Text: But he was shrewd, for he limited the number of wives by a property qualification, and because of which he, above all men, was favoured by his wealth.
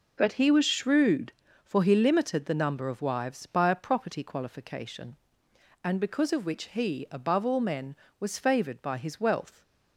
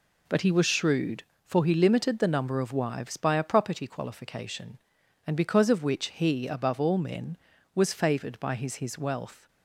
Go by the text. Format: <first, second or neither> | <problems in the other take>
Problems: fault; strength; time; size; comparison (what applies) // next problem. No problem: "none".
first | says "his" twice; at 8.7 s